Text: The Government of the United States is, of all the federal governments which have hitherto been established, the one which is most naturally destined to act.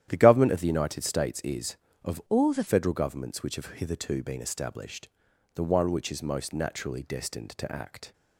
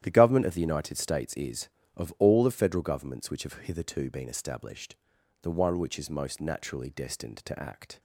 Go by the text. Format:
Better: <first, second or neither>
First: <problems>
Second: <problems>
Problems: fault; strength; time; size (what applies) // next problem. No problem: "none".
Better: second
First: starts louder than the rest; strong; until 1.1 s; 11 dB // changes voice from "all" to "the"; from 2.2 to 2.6 s; 0.4 s long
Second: starts louder than the rest; strong; until 1.0 s; 11 dB